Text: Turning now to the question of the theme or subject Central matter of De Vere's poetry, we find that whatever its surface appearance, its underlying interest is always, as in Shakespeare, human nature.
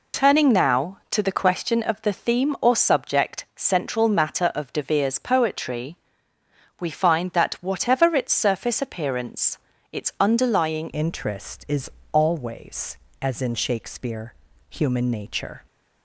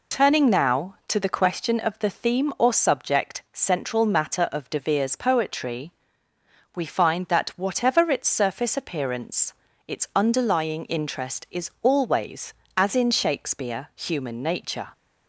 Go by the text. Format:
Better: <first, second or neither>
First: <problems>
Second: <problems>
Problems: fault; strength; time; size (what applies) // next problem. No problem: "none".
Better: second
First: changes voice at "interest"; from 10.9 s on; 4.7 s long // pauses between "is" and "always"; slight; at 11.9 s; 0.22 s long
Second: none